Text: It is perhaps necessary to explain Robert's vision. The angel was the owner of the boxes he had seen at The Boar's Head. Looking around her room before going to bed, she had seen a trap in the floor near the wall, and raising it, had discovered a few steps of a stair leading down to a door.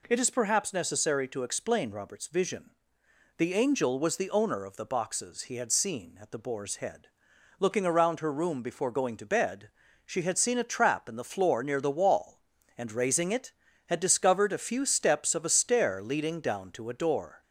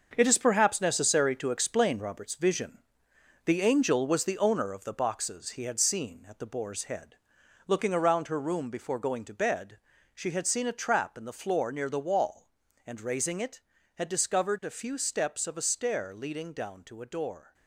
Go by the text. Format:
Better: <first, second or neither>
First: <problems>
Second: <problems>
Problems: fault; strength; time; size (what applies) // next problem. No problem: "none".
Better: first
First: none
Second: gets quieter; strong; throughout; 8.5 dB